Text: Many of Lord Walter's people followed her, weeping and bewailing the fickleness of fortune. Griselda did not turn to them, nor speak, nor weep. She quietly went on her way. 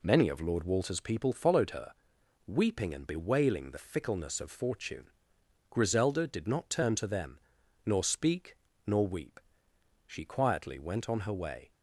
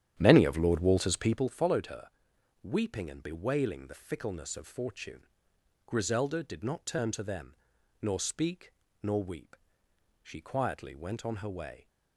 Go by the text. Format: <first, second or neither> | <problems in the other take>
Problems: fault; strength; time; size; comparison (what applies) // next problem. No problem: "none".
first | starts louder than the rest; strong; until 1.5 s; 10 dB